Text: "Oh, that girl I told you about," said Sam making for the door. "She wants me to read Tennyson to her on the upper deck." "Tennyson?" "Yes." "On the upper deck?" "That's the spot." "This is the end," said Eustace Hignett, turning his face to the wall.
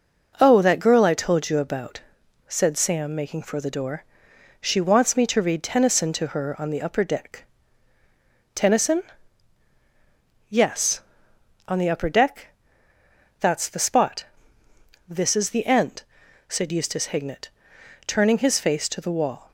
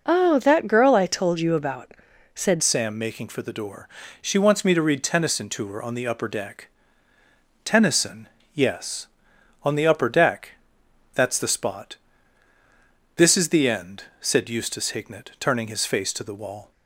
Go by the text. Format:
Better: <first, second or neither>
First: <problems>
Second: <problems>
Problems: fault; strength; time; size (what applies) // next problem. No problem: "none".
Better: first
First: none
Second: changes voice at "Sam"; from 2.6 s on; 14.1 s long